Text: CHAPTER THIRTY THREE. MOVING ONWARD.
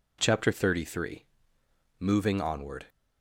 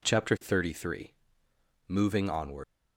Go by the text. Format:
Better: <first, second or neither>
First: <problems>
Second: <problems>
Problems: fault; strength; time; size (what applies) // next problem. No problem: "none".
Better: first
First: none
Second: leaves "ONWARD" unfinished; at 2.6 s; 130 ms